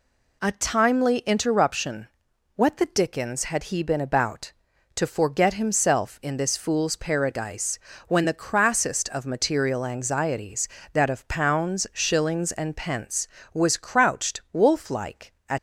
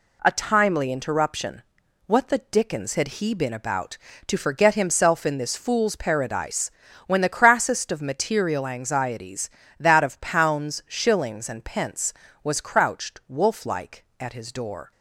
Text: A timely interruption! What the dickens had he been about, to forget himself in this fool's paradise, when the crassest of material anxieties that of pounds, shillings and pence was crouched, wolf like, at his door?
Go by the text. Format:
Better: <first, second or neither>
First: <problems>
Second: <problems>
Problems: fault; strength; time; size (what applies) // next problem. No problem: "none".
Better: second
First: stops before "his door"; at 15.5 s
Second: none